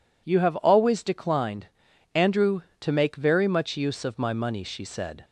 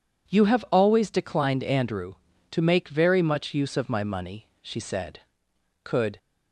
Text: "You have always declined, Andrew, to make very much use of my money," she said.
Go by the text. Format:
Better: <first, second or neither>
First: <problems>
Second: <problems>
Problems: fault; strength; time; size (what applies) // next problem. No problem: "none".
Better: first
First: none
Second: goes on to say "Could"; slight; from 5.8 s on; 0.34 s long